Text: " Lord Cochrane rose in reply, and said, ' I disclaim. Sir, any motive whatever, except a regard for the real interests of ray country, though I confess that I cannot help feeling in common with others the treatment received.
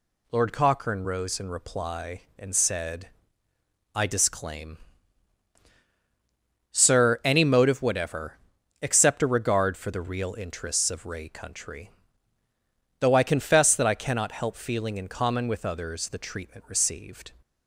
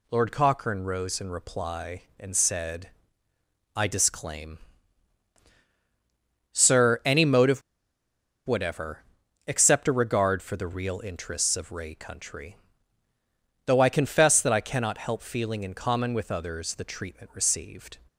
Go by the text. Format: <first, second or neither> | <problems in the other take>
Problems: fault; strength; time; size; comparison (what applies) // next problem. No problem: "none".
first | pauses between "motive" and "whatever"; noticeable; at 7.6 s; 0.86 s long